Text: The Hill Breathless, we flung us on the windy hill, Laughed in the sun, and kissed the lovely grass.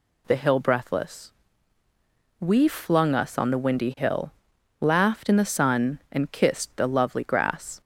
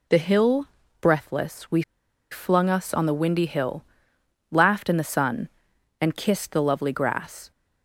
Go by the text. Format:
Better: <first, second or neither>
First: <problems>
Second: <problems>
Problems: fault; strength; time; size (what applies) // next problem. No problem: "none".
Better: first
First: none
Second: pauses between "Hill" and "Breathless"; slight; at 0.6 s; 0.36 s long // pauses between "we" and "flung"; noticeable; at 1.8 s; 0.49 s long